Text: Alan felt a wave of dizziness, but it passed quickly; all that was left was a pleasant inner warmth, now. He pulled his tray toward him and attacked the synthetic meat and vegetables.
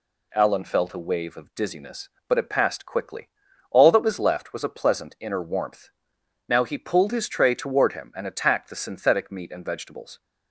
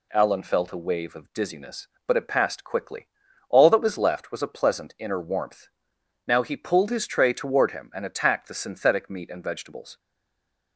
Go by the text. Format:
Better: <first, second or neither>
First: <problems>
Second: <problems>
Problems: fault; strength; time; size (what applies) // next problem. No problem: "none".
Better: first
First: none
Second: stays silent after the last word; slight; from 9.9 s on; 0.8 s long